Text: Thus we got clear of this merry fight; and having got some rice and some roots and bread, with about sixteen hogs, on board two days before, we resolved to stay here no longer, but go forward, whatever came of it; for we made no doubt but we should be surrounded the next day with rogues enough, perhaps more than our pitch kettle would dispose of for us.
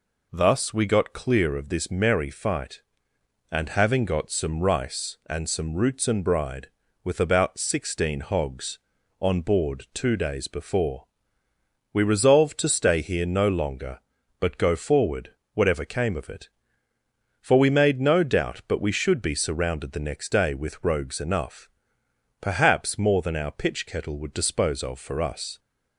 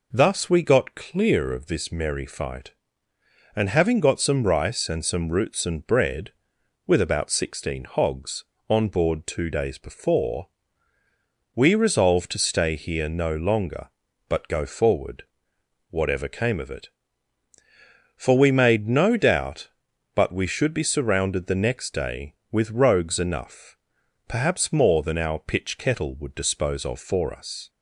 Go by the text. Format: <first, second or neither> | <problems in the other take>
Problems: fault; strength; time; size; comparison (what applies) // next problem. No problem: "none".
second | says "bride" for "bread"; at 6.2 s